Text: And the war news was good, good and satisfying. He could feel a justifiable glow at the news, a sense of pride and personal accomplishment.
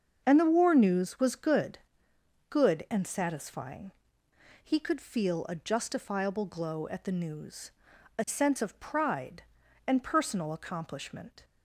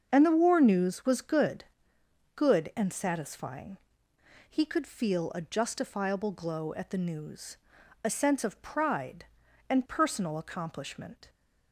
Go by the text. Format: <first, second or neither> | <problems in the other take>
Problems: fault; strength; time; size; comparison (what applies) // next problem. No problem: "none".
neither | starts louder than the rest; the same in both